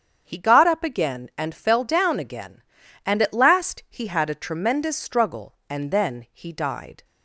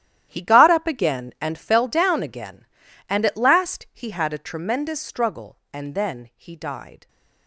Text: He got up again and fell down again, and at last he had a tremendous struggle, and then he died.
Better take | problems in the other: first | gets quieter; strong; throughout; 14 dB // starts louder than the rest; strong; until 1.3 s; 12 dB; strong in the first

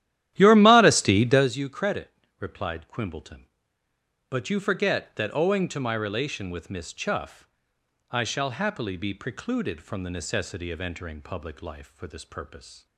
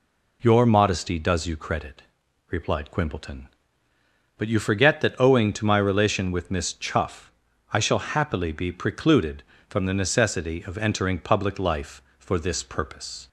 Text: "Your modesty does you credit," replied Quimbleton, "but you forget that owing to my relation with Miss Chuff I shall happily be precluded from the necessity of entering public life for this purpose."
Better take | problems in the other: second | starts louder than the rest; strong; until 1.5 s; 12.5 dB // pauses between "Chuff" and "I"; noticeable; at 7.4 s; 0.62 s long; also in the second

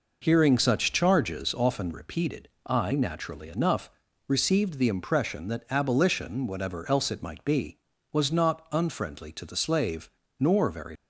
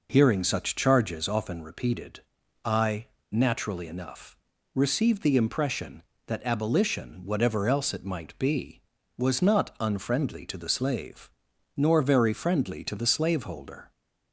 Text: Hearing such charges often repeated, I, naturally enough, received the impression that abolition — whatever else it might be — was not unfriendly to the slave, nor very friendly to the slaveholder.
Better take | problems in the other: second | stops before "friendly to the slaveholder"; at 10.9 s

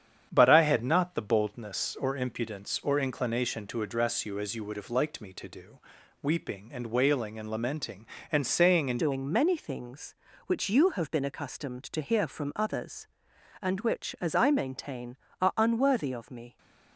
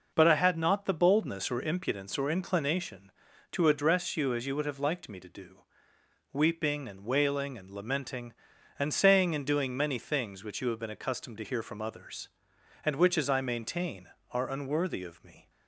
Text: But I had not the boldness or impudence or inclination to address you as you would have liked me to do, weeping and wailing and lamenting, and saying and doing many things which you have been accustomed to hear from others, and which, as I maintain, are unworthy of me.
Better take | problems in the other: second | starts louder than the rest; strong; until 1.3 s; 8.5 dB // changes voice at "doing"; from 8.9 s on; 7.6 s long

